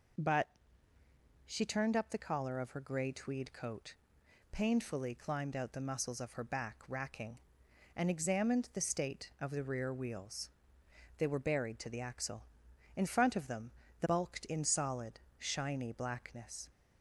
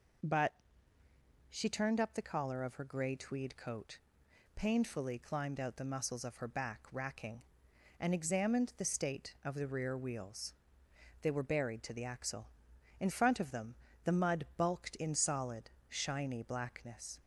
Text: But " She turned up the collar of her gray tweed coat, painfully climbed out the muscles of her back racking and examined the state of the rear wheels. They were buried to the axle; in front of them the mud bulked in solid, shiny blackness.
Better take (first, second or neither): second